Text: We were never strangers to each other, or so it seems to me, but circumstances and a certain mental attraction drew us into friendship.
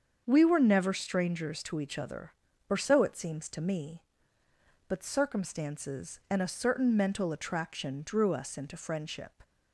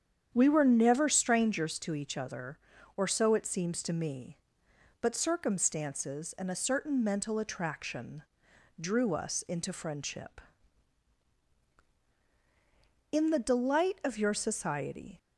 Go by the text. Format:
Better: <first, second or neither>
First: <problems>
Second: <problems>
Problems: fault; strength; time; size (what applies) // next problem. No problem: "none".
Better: first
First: starts louder than the rest; until 1.2 s; 7 dB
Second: starts louder than the rest; strong; until 1.3 s; 8.5 dB // pauses between "attraction" and "drew"; noticeable; at 8.2 s; 0.58 s long // goes on to say "In the delight of your society"; strong; from 13.1 s on; 2.0 s long